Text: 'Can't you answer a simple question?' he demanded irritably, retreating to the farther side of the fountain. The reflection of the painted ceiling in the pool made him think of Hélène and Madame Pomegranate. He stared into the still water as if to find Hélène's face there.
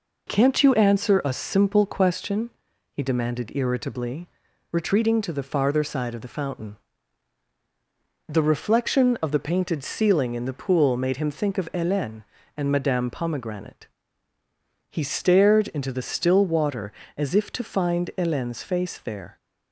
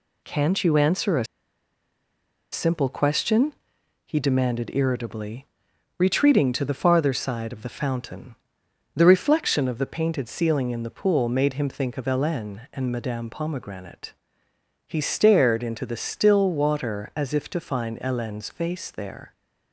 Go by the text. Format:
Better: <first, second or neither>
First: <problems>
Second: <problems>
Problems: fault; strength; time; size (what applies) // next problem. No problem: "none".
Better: first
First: none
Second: pauses between "a" and "simple"; strong; at 1.2 s; 1.2 s long